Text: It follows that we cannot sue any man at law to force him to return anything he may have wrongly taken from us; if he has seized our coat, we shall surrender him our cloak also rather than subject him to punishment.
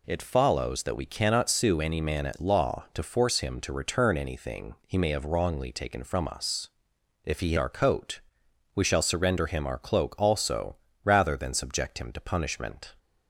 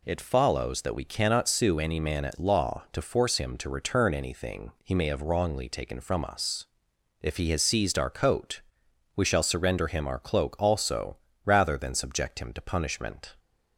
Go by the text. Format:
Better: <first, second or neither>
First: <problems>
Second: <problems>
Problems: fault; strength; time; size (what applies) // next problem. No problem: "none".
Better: second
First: skips "has seized"; at 7.5 s // pauses between "also" and "rather"; slight; at 10.7 s; 0.28 s long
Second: pauses between "also" and "rather"; slight; at 11.1 s; 0.28 s long